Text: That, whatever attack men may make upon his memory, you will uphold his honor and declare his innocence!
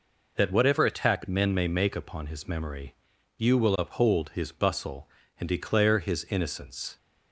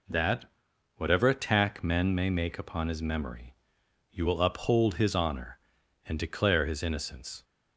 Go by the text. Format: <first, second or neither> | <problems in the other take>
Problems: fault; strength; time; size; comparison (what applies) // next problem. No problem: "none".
second | says "bustle" for "honor"; at 4.5 s